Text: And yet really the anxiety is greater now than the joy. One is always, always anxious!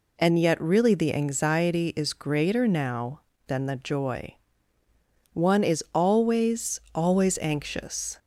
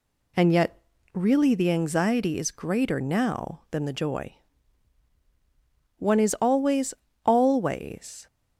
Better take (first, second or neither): first